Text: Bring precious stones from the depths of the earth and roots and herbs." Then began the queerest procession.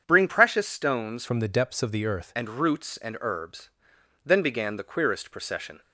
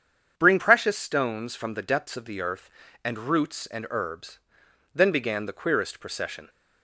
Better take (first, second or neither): second